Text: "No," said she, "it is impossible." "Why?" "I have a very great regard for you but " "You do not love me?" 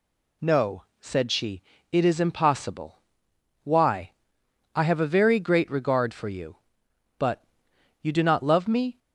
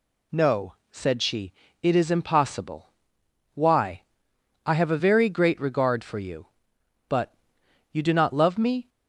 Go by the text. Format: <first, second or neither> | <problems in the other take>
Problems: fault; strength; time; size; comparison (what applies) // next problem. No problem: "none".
neither | none